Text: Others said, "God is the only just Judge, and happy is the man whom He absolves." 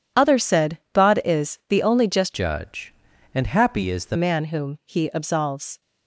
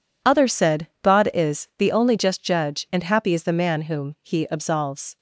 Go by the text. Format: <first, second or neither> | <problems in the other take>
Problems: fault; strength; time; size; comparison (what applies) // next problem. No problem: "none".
second | changes voice from "Judge" to "the"; from 2.3 to 4.1 s; 1.8 s long